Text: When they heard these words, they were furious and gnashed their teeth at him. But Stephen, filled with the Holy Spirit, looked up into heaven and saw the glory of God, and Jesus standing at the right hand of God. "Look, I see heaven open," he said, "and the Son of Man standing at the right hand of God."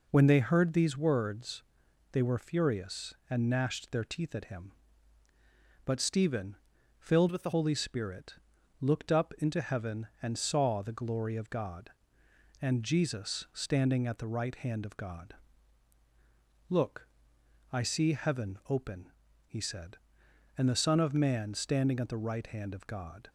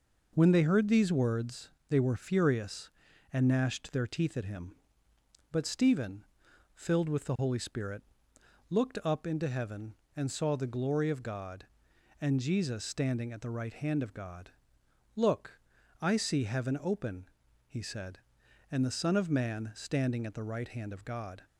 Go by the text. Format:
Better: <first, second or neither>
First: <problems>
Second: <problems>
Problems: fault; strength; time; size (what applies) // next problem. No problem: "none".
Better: second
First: changes voice from "with" to "the"; from 7.3 to 7.5 s; 0.2 s long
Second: none